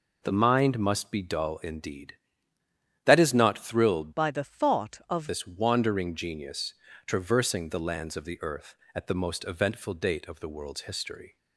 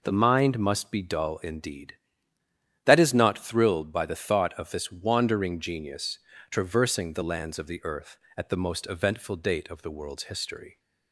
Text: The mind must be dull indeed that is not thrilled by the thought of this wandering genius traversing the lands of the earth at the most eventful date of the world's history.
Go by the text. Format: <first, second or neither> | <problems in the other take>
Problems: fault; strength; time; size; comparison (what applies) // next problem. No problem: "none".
second | changes voice from "by" to "of"; from 4.1 to 5.2 s; 1.1 s long // pauses between "genius" and "traversing"; slight; at 6.7 s; 0.32 s long; slight in the second